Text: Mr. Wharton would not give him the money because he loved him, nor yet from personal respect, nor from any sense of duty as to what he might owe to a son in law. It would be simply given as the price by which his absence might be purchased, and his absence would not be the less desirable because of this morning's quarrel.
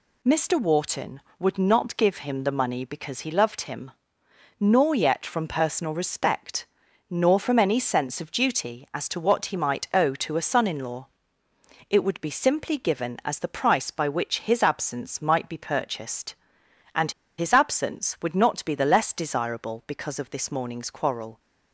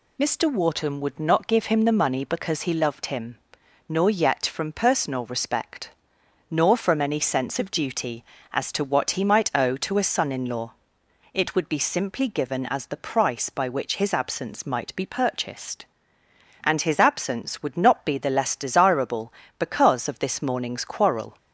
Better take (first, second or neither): second